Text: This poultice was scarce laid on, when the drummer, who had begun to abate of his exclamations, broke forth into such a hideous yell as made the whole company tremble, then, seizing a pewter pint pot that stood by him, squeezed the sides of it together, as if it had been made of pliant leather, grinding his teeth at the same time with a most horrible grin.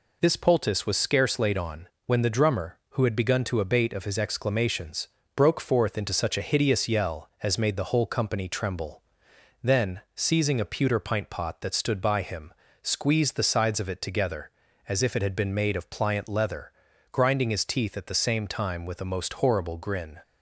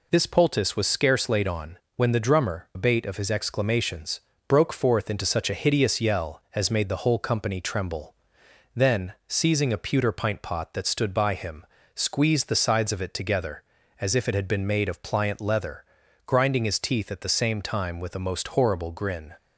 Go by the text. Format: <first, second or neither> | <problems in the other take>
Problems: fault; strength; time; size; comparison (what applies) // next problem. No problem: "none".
first | skips "who had begun to"; at 2.7 s